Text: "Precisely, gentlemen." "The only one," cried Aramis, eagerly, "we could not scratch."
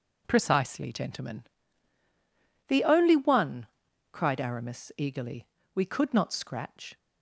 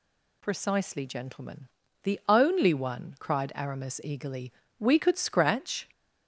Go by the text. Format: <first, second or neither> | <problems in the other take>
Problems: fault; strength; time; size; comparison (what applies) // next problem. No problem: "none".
first | skips "not"; at 5.1 s